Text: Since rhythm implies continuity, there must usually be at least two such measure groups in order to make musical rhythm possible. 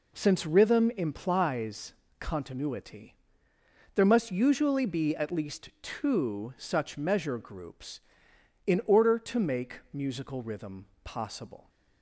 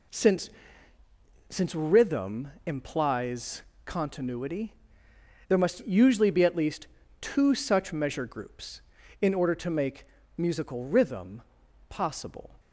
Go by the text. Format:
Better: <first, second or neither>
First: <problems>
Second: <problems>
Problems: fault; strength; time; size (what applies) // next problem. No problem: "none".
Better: first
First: pauses between "implies" and "continuity"; slight; at 1.9 s; 0.28 s long // pauses between "rhythm" and "possible"; slight; at 10.8 s; 0.18 s long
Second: says "Since" twice; at 1.5 s // pauses between "implies" and "continuity"; slight; at 3.6 s; 0.22 s long // pauses between "least" and "two"; slight; at 6.8 s; 0.34 s long // pauses between "make" and "musical"; slight; at 10.0 s; 0.32 s long // pauses between "rhythm" and "possible"; noticeable; at 11.4 s; 0.46 s long